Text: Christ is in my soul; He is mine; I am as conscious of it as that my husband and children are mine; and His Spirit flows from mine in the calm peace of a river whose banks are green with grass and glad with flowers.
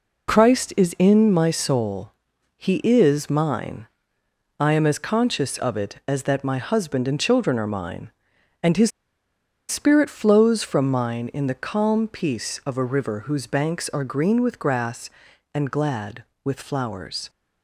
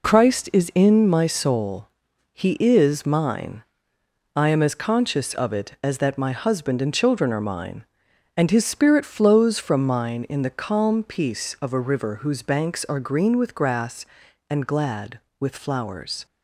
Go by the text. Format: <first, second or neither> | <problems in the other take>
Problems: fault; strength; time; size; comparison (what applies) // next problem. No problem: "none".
second | pauses between "His" and "Spirit"; noticeable; at 8.9 s; 0.78 s long